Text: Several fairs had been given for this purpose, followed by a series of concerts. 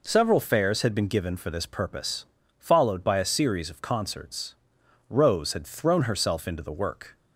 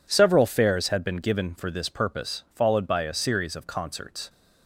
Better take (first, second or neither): second